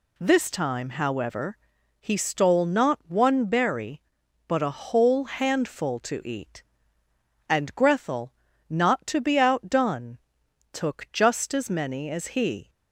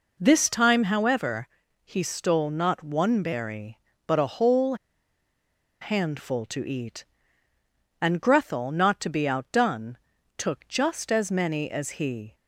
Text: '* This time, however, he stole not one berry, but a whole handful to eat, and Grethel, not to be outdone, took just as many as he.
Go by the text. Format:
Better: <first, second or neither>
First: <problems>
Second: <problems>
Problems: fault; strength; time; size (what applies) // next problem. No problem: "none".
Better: first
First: none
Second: pauses between "whole" and "handful"; at 4.7 s; 1.0 s long